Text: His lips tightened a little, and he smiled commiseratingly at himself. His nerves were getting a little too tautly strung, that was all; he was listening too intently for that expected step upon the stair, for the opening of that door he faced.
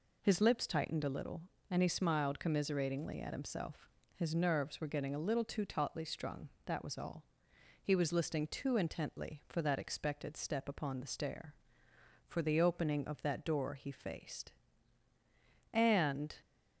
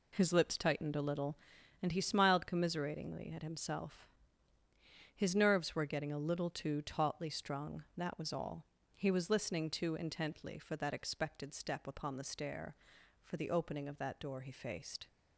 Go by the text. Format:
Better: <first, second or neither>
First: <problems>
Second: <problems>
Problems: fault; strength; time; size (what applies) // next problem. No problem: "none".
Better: second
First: goes on to say "And"; noticeable; from 15.7 s on; 0.62 s long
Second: none